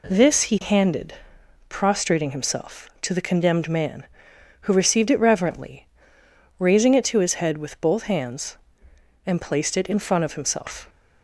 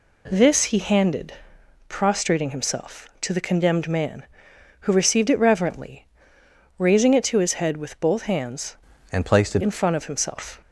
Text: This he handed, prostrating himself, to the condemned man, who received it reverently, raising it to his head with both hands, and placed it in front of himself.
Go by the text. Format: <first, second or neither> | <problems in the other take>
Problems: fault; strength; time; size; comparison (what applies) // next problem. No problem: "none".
first | changes voice from "and" to "it"; from 9.1 to 9.6 s; 0.5 s long